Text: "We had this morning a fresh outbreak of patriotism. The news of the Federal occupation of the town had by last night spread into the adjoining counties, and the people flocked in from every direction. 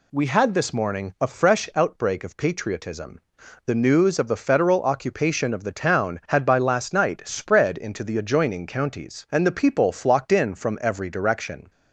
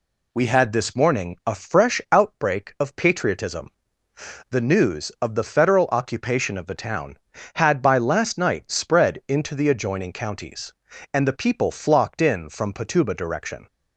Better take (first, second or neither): first